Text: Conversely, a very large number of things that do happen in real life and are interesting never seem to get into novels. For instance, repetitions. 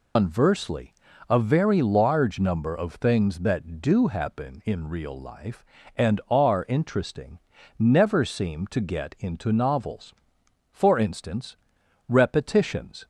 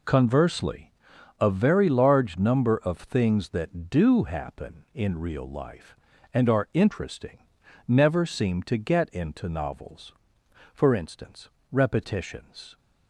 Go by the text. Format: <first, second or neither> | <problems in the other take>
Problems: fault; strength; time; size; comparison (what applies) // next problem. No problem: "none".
second | loses the start of "Conversely"; at 0.1 s; 160 ms // pauses between "interesting" and "never"; at 7.3 s; 0.40 s long; noticeable in the second